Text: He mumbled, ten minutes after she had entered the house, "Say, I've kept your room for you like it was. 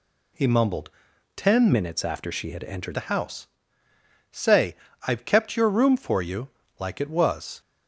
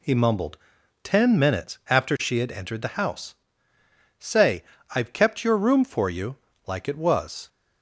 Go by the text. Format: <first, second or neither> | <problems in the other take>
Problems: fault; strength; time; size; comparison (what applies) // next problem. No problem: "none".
second | changes voice from "minutes" to "entered"; from 1.7 to 2.9 s; 1.2 s long // pauses between "you" and "like"; slight; at 6.4 s; 0.30 s long; slight in the second